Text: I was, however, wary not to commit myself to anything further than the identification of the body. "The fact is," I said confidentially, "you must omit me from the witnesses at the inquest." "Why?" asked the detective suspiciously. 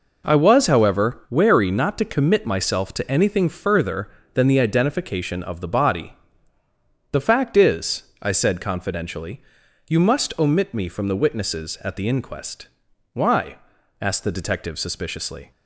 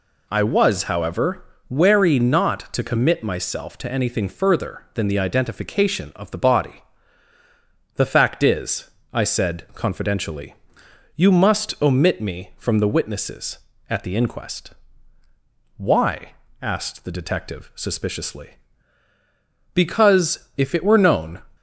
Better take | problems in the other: first | goes on to say "Because if it were known"; strong; from 19.7 s on; 1.6 s long

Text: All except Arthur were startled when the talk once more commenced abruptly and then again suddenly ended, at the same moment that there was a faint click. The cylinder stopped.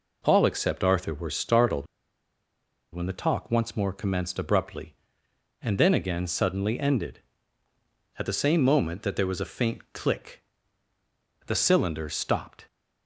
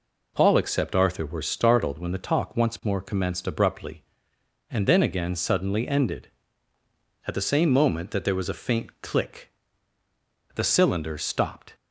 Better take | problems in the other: second | pauses between "startled" and "when"; at 1.8 s; 1.0 s long

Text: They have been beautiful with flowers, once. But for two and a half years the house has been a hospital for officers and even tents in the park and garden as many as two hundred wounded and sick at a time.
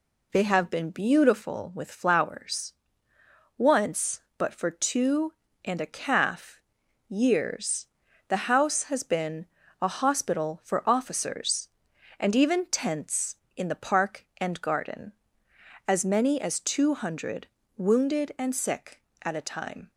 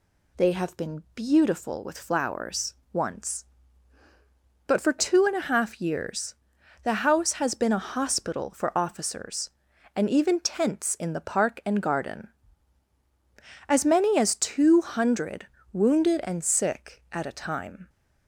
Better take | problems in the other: second | says "calf" for "half"; at 5.8 s // pauses between "years" and "the"; at 7.8 s; 0.42 s long; noticeable in the second // pauses between "been" and "a"; at 9.4 s; 0.38 s long // pauses between "hundred" and "wounded"; slight; at 17.4 s; 0.28 s long; slight in the second

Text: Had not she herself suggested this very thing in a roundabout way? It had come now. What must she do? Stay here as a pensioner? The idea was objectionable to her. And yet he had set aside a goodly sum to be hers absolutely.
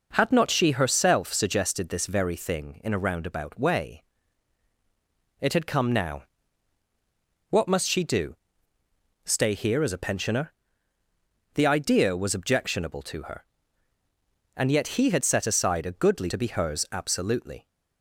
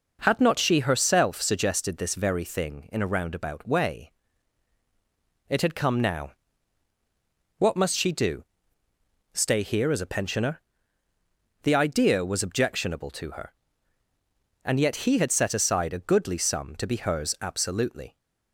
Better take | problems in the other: second | skips "sum"; at 16.2 s

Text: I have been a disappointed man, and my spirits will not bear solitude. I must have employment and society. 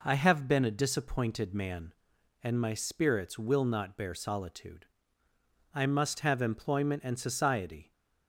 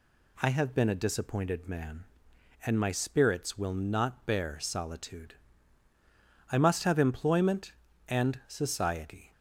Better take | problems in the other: neither | none

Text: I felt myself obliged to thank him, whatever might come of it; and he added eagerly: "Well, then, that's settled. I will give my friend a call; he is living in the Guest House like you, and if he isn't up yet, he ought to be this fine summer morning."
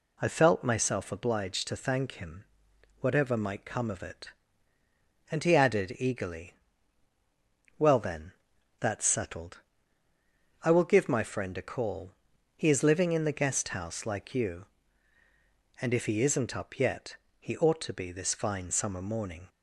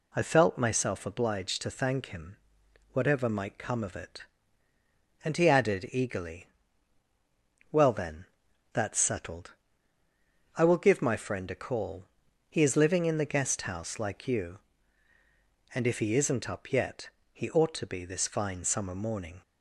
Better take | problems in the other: neither | none

